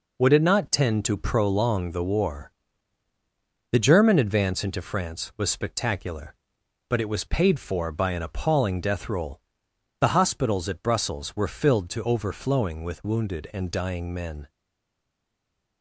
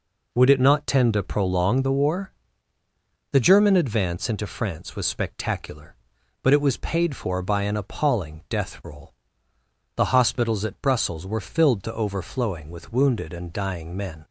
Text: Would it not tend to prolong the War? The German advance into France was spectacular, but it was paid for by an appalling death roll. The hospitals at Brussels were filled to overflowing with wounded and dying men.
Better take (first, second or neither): second